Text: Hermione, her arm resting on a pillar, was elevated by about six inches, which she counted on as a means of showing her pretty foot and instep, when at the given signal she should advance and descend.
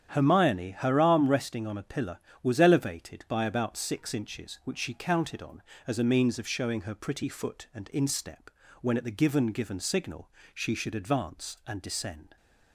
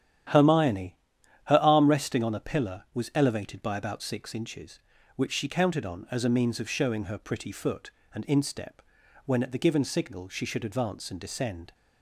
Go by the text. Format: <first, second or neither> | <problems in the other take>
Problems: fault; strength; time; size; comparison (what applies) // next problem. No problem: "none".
second | starts louder than the rest; strong; until 1.2 s; 9.5 dB; strong in the second // says "given" twice; at 9.4 s // pauses between "signal" and "she"; slight; at 10.3 s; 0.24 s long